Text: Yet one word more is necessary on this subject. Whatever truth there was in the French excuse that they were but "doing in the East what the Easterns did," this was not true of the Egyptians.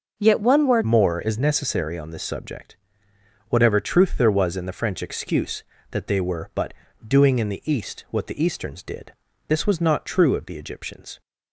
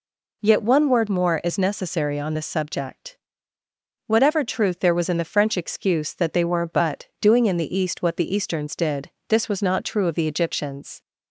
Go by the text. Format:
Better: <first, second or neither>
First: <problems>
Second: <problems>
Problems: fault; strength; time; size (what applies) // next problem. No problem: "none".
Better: second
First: changes voice at "more"; from 0.8 s on; 10.4 s long // pauses between "but" and "doing"; slight; at 6.7 s; 0.34 s long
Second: none